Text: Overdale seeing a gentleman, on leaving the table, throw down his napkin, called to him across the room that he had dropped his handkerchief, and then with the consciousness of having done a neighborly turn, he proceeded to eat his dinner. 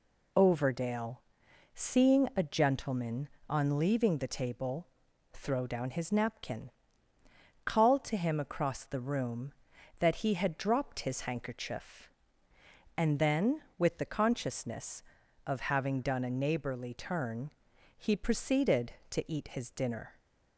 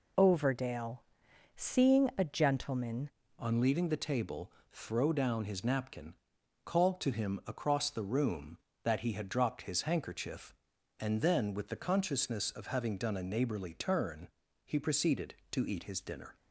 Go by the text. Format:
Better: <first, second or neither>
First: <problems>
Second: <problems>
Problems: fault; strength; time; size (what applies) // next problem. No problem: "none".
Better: first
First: pauses between "Overdale" and "seeing"; noticeable; at 1.1 s; 0.56 s long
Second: pauses between "Overdale" and "seeing"; noticeable; at 0.9 s; 0.56 s long // changes voice at "on"; from 3.3 s on; 13.0 s long